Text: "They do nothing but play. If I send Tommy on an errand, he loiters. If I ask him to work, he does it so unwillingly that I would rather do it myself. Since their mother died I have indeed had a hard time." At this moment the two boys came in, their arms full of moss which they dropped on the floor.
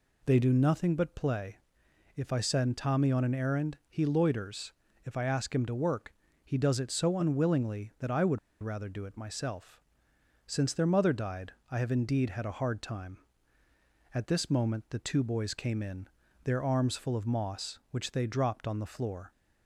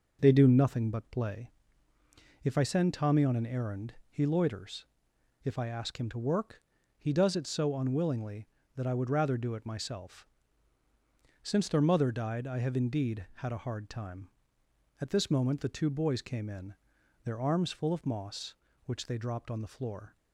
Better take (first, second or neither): second